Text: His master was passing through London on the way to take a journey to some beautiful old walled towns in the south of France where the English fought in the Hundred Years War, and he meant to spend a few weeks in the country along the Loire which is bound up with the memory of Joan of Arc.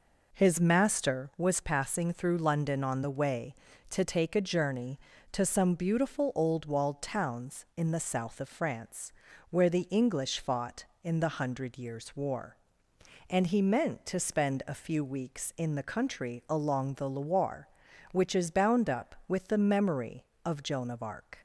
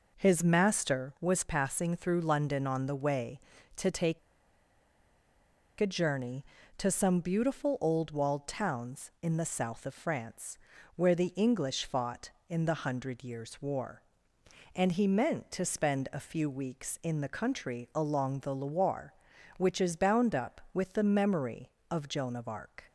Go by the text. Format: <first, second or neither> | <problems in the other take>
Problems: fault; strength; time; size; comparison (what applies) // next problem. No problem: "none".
first | pauses between "take" and "a"; strong; at 4.1 s; 1.6 s long // pauses between "France" and "where"; at 10.5 s; 0.38 s long; also in the first